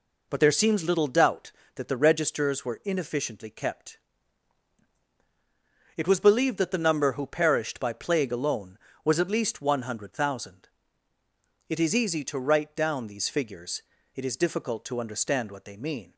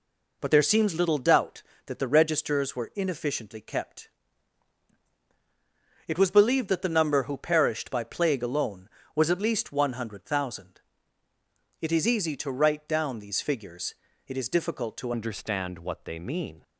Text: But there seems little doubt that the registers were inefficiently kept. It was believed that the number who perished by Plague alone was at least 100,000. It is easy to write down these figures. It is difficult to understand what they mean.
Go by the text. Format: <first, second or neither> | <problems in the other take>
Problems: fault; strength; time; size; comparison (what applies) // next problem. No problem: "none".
first | changes voice at "understand"; from 15.1 s on; 1.5 s long